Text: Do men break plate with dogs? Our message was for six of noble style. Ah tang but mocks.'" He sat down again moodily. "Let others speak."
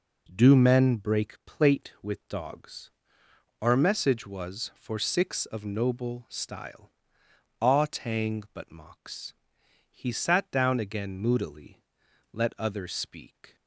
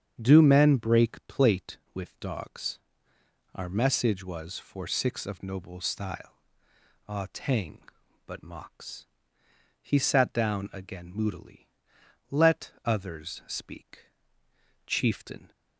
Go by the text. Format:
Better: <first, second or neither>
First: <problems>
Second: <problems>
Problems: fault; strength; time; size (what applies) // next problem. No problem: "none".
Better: first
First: none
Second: starts louder than the rest; strong; until 1.3 s; 8 dB // goes on to say "Chieftain"; noticeable; from 14.8 s on; 0.64 s long